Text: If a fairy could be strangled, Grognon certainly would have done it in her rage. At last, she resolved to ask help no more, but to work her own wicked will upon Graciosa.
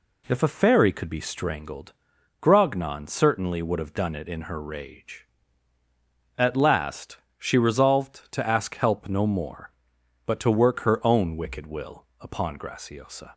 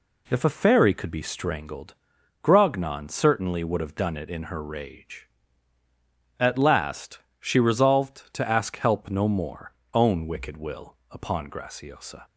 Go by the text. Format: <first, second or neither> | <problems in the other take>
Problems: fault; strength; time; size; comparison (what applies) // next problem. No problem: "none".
first | skips "but to work her"; at 9.8 s // pauses between "will" and "upon"; slight; at 10.9 s; 0.16 s long; slight in the first